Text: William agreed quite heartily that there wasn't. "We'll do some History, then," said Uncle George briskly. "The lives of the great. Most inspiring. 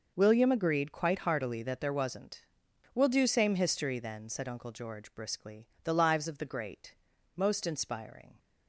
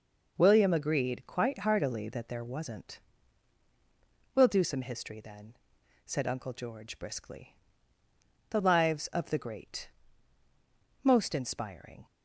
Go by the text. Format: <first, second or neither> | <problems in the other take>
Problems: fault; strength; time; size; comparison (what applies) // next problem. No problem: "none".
second | says "same" for "some"; at 3.2 s